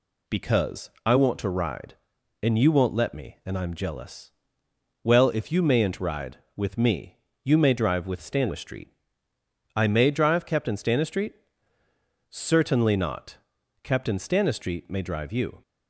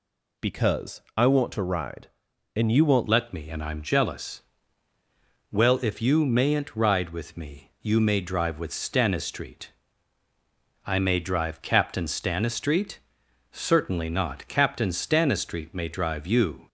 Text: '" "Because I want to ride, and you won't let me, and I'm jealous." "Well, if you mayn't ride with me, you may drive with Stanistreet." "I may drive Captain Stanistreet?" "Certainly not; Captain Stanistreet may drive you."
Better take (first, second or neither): first